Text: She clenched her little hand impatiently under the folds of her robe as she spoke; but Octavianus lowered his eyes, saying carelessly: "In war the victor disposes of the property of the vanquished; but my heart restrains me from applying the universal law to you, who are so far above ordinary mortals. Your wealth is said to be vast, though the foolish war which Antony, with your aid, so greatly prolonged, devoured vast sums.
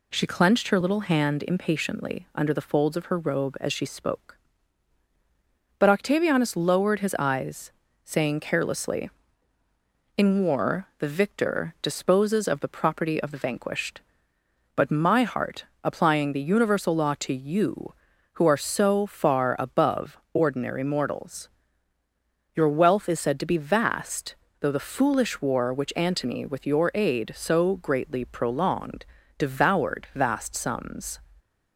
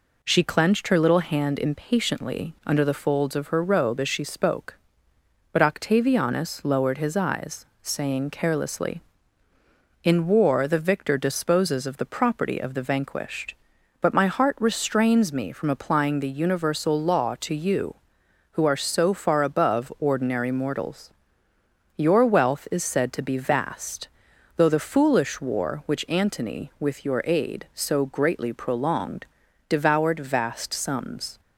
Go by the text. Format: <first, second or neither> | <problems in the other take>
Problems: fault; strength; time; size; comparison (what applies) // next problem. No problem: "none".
second | skips "restrains me from"; at 15.7 s // pauses between "above" and "ordinary"; slight; at 20.1 s; 0.16 s long